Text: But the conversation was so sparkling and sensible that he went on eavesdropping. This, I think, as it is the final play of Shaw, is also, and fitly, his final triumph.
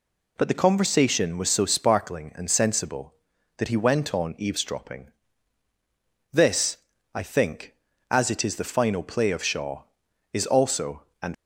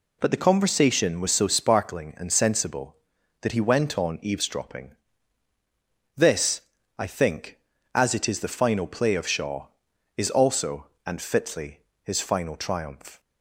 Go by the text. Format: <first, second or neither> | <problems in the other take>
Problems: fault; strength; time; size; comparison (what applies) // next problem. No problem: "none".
second | stops before "fitly his final triumph"; at 11.3 s